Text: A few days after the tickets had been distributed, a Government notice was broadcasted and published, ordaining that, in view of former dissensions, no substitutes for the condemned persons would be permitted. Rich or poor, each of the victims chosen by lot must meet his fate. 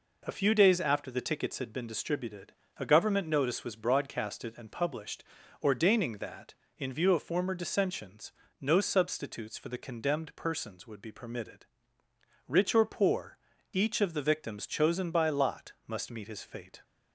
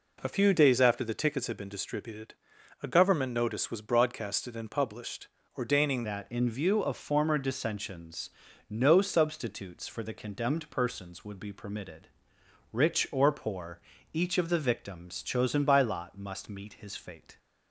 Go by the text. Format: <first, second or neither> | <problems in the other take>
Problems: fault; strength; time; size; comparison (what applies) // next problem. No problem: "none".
first | changes voice at "that"; from 6.0 s on; 11.3 s long